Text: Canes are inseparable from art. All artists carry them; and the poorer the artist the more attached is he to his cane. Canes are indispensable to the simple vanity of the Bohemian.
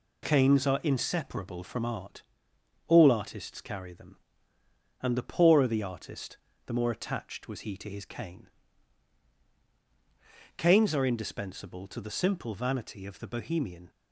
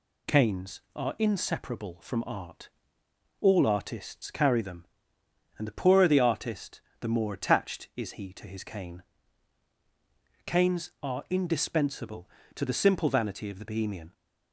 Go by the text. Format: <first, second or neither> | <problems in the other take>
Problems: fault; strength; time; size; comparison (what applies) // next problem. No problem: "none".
second | pauses between "artist" and "the"; slight; at 6.3 s; 0.26 s long; slight in the second // says "was" for "is"; at 7.4 s